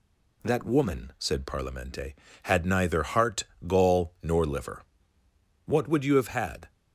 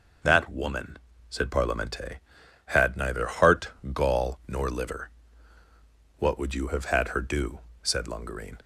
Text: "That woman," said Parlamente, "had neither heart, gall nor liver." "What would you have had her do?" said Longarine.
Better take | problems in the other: second | stops before "her do said Longarine"; at 6.6 s

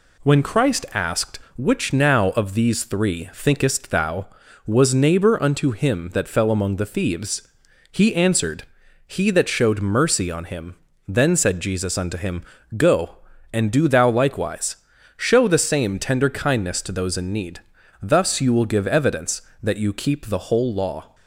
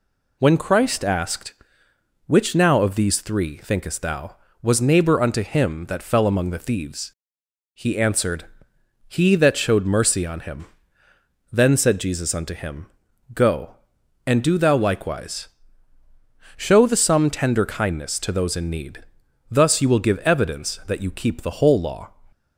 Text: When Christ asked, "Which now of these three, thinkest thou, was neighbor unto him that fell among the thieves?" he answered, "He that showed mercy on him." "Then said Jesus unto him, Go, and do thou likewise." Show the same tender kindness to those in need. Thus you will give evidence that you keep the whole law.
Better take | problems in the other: first | says "some" for "same"; at 16.9 s

